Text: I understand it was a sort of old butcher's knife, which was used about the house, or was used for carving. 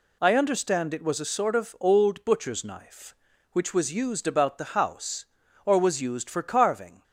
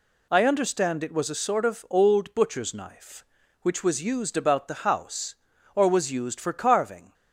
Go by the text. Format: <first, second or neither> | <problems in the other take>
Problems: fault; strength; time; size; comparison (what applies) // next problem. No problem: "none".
neither | none